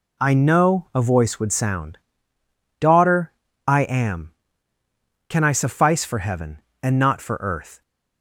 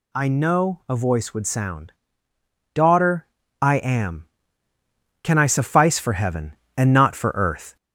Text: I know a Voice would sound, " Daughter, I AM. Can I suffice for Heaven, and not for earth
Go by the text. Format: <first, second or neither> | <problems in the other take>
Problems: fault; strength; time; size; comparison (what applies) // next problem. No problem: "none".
first | gets louder; strong; throughout; 7.5 dB